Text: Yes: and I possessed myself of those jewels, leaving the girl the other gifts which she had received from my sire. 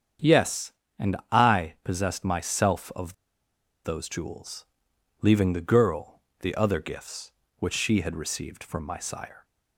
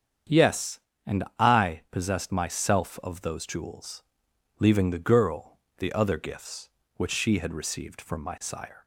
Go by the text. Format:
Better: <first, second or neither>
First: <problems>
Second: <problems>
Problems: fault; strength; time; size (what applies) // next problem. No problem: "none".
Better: second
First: starts louder than the rest; strong; until 1.6 s; 8 dB // pauses between "and" and "I"; slight; at 1.1 s; 0.16 s long // pauses between "of" and "those"; noticeable; at 3.1 s; 0.70 s long // pauses between "girl" and "the"; slight; at 6.2 s; 0.20 s long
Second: starts louder than the rest; strong; until 1.7 s; 8 dB // pauses between "and" and "I"; slight; at 1.2 s; 0.16 s long // pauses between "girl" and "the"; slight; at 5.5 s; 0.20 s long